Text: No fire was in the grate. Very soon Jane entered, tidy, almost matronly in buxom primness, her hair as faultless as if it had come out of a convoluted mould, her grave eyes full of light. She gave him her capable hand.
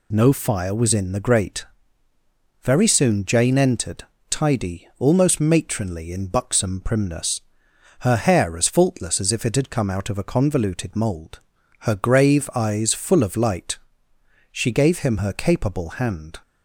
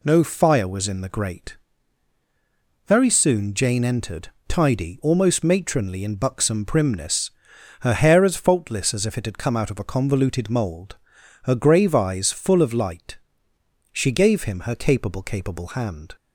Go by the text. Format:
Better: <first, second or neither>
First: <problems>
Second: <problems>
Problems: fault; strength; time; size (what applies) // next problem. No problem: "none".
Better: first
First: none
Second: says "capable" twice; at 15.2 s